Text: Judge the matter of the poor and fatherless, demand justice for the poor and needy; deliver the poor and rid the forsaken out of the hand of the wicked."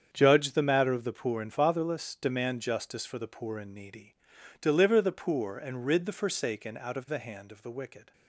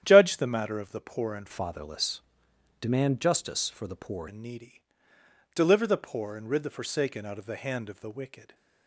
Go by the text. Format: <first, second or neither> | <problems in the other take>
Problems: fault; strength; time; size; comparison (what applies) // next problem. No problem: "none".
first | starts louder than the rest; strong; until 1.0 s; 10 dB; strong in the first // changes voice from "fatherless" to "poor"; from 1.5 to 4.2 s; 2.7 s long